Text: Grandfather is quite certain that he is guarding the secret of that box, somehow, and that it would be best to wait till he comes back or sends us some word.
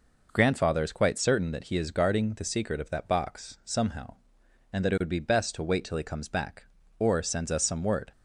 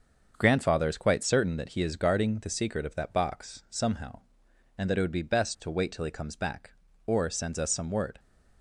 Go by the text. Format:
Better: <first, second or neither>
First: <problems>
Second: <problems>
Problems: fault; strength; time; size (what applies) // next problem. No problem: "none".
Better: first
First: none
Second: gets quieter; noticeable; throughout; 6 dB